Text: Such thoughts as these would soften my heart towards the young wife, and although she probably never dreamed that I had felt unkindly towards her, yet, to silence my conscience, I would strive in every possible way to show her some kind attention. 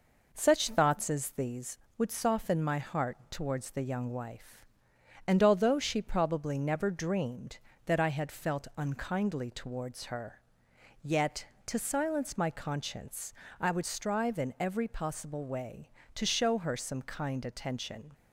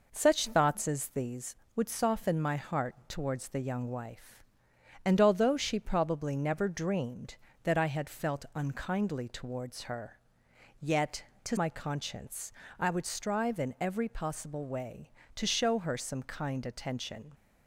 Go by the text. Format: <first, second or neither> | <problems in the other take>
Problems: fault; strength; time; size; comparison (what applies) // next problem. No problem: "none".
first | skips "silence"; at 11.5 s